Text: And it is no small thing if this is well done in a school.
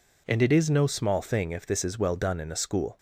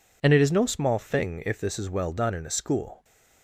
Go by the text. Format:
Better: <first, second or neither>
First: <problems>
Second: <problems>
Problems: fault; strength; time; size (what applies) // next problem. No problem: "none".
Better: neither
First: none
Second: none